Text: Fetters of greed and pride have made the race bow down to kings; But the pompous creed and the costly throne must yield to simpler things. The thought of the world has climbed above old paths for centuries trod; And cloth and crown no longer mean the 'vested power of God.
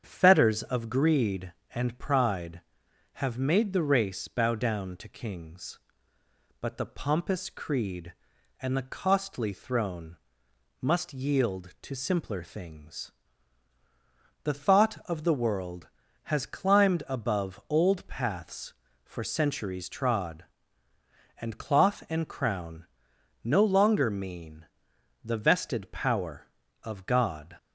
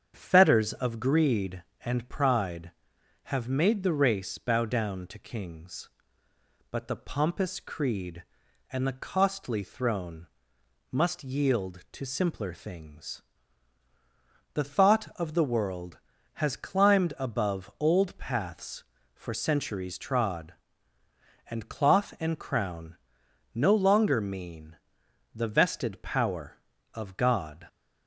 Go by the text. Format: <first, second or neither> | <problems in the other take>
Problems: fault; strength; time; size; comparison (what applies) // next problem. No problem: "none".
neither | starts louder than the rest; strong; the same in both // pauses between "throne" and "must"; noticeable; the same in both // pauses between "crown" and "no"; noticeable; the same in both // pauses between "mean" and "the"; noticeable; the same in both